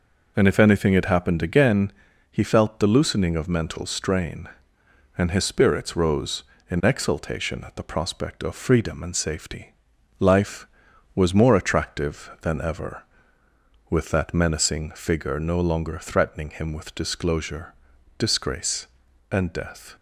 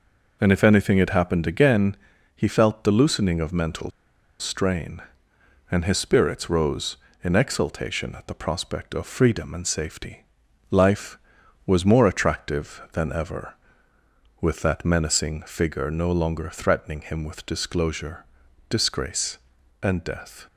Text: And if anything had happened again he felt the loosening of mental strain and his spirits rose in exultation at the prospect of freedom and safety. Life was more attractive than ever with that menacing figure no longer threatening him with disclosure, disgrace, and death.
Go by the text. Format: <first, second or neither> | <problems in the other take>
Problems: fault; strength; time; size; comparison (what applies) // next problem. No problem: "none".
first | pauses between "again" and "he"; at 1.9 s; 0.38 s long; also in the first // pauses between "mental" and "strain"; noticeable; at 3.8 s; 0.51 s long